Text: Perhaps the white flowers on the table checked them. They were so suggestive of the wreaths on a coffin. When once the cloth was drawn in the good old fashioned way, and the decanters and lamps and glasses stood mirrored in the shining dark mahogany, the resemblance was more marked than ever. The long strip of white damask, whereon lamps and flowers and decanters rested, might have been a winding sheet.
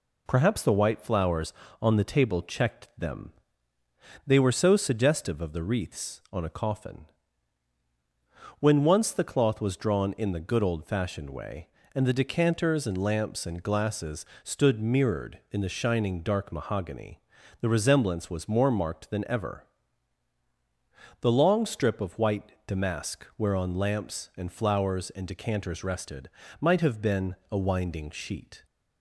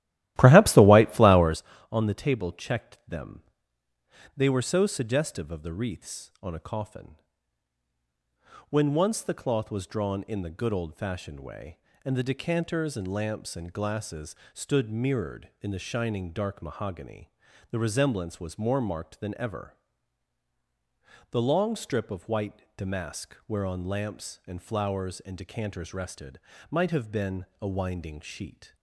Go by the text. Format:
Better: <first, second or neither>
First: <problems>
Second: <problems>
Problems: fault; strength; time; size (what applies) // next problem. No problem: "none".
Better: first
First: pauses between "glasses" and "stood"; slight; at 14.2 s; 0.18 s long // pauses between "white" and "damask"; slight; at 22.5 s; 0.16 s long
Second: starts louder than the rest; strong; until 1.7 s; 14.5 dB // pauses between "glasses" and "stood"; slight; at 14.3 s; 0.18 s long // pauses between "white" and "damask"; slight; at 22.6 s; 0.16 s long